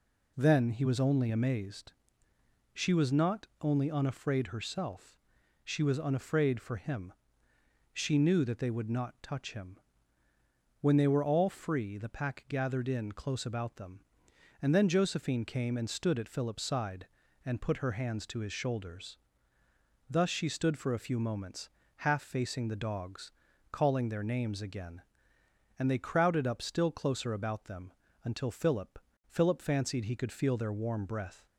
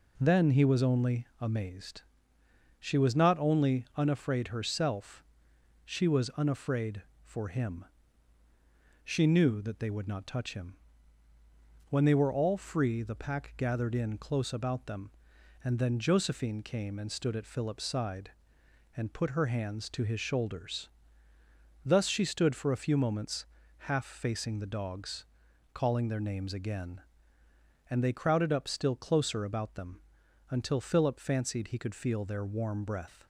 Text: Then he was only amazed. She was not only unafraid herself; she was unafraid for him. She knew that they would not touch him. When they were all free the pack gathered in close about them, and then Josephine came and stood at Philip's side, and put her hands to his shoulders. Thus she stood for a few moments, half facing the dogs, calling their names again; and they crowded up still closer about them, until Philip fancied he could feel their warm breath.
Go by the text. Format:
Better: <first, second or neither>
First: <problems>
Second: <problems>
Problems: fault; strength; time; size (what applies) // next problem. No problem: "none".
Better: second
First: says "Philip" twice; at 29.2 s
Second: none